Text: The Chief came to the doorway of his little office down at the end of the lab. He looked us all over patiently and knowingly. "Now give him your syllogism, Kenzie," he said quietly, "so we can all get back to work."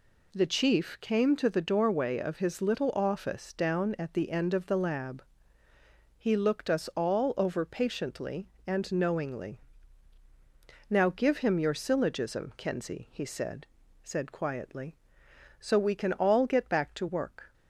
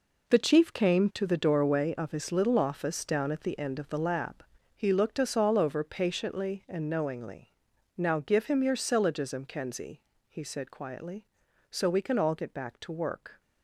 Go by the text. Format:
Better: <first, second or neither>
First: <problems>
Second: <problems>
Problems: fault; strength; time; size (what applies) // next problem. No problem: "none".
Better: second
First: says "said" twice; at 14.0 s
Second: none